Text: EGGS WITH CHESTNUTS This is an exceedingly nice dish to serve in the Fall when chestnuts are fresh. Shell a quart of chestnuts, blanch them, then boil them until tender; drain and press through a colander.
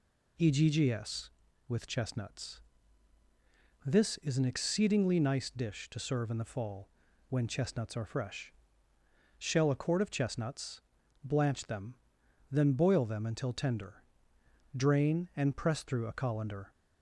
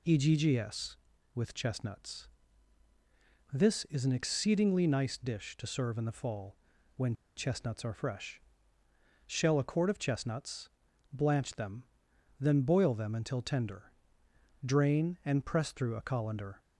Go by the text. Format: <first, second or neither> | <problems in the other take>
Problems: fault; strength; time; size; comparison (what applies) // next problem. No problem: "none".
first | pauses between "CHESTNUTS" and "This"; at 2.2 s; 1.2 s long; also in the first // pauses between "Fall" and "when"; at 6.5 s; 0.40 s long; also in the first // pauses between "when" and "chestnuts"; slight; at 7.1 s; 0.22 s long